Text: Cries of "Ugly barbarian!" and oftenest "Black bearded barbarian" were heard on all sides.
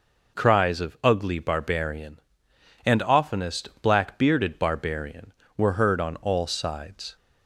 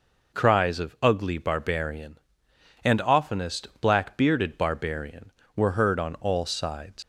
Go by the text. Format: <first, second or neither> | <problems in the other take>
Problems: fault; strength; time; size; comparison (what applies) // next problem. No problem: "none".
first | leaves "sides" unfinished; at 7.0 s; 115 ms